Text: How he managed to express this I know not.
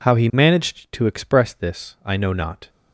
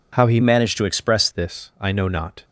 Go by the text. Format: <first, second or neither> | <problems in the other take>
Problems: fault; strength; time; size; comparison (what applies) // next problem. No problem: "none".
first | changes voice from "managed" to "express"; from 0.4 to 1.2 s; 0.8 s long